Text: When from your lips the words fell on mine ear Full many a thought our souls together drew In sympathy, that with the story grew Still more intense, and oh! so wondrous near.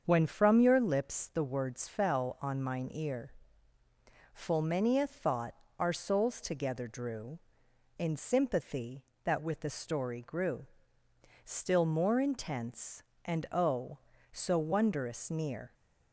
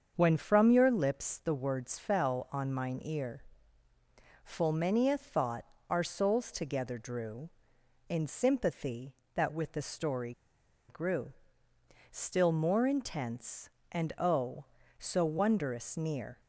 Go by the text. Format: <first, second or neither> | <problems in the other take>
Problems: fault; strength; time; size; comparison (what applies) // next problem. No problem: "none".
first | starts louder than the rest; until 1.1 s; 7 dB; also in the first // pauses between "ear" and "Full"; at 3.4 s; 1.0 s long; also in the first // pauses between "thought" and "our"; slight; at 5.6 s; 0.24 s long; slight in the first // pauses between "story" and "grew"; noticeable; at 10.3 s; 0.57 s long // pauses between "grew" and "Still"; noticeable; at 11.3 s; 0.80 s long; noticeable in the first